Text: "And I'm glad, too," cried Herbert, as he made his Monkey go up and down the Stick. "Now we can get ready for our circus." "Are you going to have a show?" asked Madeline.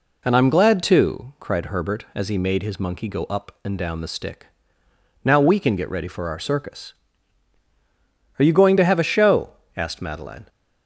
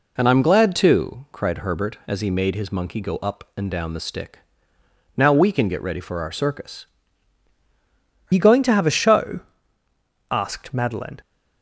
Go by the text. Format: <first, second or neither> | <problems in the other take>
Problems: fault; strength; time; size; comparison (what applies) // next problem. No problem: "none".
first | changes voice at "you"; from 8.3 s on; 2.9 s long